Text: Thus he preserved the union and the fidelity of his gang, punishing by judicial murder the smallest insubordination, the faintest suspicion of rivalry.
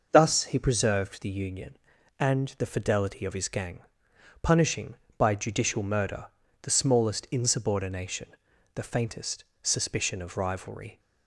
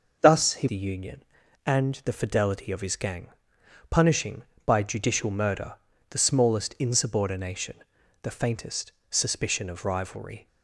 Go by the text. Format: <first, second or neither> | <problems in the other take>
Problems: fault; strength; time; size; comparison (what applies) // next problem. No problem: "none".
first | skips "preserved"; at 0.6 s // pauses between "murder" and "the"; slight; at 5.7 s; 0.34 s long; slight in the first // pauses between "faintest" and "suspicion"; slight; at 8.9 s; 0.18 s long; slight in the first